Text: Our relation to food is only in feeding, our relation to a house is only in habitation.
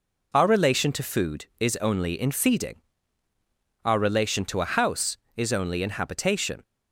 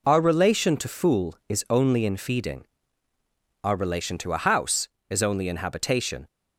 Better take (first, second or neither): first